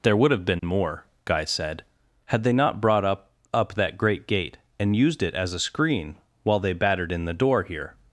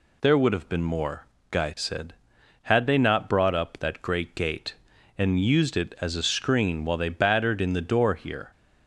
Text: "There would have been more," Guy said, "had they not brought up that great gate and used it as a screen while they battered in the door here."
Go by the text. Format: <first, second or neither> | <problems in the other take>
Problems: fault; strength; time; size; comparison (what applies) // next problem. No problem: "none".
second | says "up" twice; at 3.5 s // pauses between "screen" and "while"; slight; at 6.1 s; 0.26 s long